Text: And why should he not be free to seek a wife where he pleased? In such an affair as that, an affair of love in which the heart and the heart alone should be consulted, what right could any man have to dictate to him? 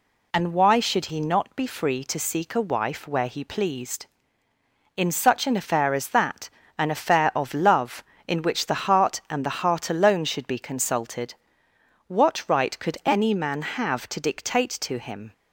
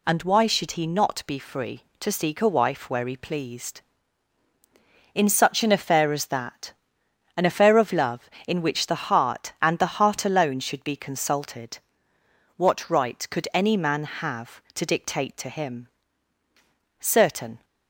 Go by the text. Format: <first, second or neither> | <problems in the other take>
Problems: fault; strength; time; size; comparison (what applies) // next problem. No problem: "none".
first | goes on to say "Certain"; noticeable; from 16.9 s on; 0.64 s long